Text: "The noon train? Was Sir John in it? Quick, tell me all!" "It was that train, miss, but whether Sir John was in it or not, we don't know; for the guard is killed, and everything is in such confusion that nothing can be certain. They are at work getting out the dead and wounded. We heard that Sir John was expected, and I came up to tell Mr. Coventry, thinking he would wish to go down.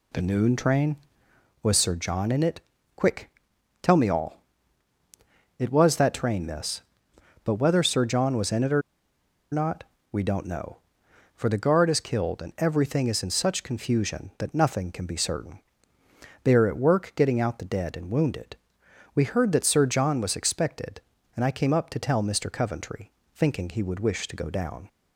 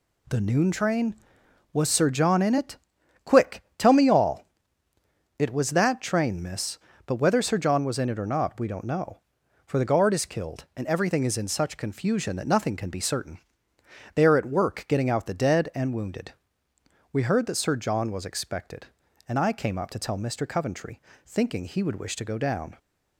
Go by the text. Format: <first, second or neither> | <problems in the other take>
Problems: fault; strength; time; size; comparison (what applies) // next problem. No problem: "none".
second | pauses between "or" and "not"; noticeable; at 8.8 s; 0.70 s long